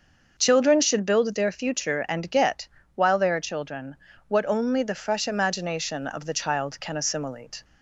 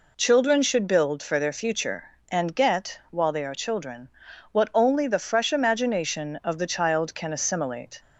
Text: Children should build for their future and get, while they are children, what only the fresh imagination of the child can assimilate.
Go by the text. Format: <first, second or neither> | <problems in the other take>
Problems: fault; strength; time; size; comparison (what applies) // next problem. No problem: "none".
second | starts louder than the rest; until 1.4 s; 6.5 dB // skips "for"; at 1.3 s